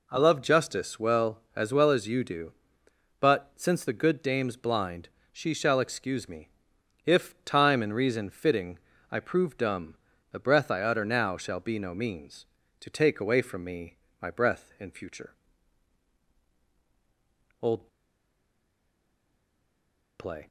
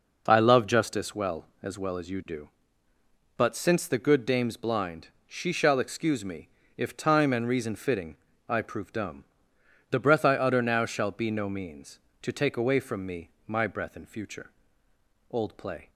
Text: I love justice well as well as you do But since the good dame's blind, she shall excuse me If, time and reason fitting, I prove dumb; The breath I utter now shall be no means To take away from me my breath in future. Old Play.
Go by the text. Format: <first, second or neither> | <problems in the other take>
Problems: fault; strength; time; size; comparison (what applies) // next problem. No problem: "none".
second | pauses between "me" and "If"; noticeable; at 6.4 s; 0.56 s long; slight in the second // pauses between "me" and "my"; slight; at 13.9 s; 0.26 s long; slight in the second // pauses between "Old" and "Play"; strong; at 17.8 s; 2.3 s long